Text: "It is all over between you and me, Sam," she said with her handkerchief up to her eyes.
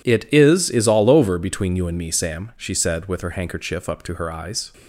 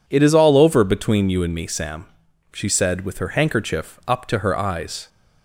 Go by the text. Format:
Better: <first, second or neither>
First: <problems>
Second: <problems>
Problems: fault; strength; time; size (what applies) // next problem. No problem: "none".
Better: second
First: says "is" twice; at 0.6 s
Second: none